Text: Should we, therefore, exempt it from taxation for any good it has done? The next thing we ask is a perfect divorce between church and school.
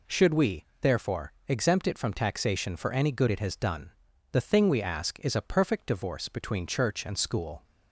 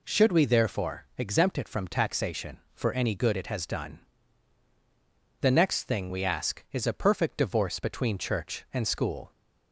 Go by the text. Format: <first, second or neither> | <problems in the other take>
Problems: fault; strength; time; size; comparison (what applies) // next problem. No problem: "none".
second | skips "next"; at 4.4 s